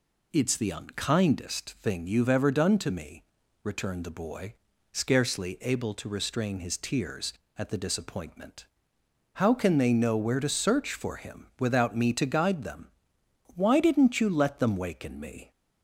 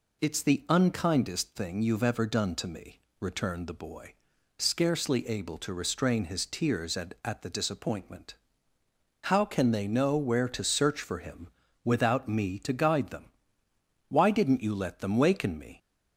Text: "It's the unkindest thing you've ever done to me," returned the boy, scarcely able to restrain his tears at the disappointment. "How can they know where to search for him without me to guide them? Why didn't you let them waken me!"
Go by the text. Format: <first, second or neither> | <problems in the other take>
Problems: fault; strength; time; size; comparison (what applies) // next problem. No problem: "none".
first | says "at" twice; at 7.2 s // pauses between "him" and "without"; at 11.4 s; 0.38 s long